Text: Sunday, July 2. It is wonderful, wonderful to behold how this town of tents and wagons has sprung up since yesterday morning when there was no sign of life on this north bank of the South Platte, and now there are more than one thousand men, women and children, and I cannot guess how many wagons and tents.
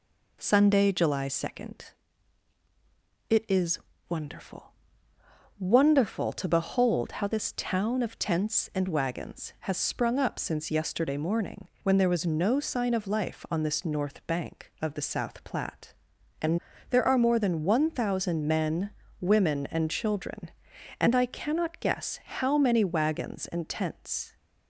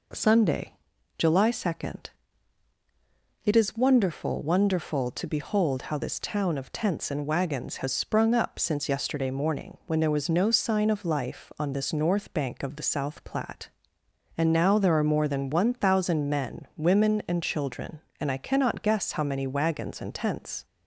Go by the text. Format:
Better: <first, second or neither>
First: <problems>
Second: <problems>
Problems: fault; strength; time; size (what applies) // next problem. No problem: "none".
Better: second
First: pauses between "is" and "wonderful"; slight; at 3.7 s; 0.30 s long // pauses between "morning" and "when"; slight; at 11.6 s; 0.16 s long // skips "now"; at 16.7 s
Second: none